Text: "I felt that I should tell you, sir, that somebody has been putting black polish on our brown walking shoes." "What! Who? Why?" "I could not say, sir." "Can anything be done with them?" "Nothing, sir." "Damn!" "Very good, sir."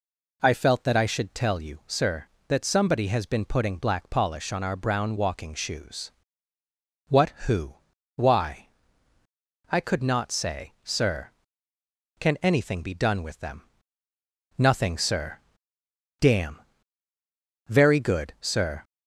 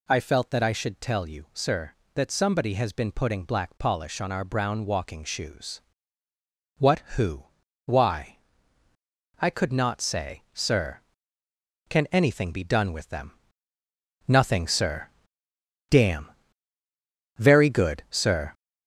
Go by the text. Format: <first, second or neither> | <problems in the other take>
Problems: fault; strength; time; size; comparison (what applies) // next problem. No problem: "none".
first | gets louder; noticeable; throughout; 6 dB